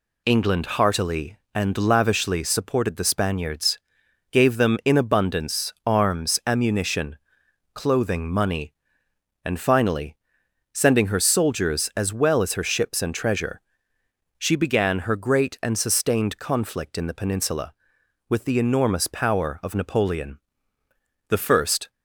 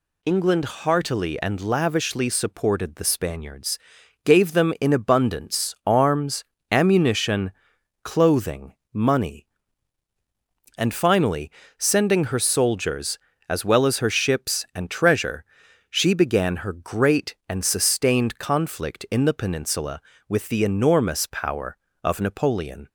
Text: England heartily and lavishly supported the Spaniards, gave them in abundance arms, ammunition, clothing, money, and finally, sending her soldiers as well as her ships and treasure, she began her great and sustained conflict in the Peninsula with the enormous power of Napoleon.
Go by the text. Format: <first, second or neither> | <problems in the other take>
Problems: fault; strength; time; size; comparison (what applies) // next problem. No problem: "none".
second | goes on to say "The first"; noticeable; from 21.2 s on; 0.62 s long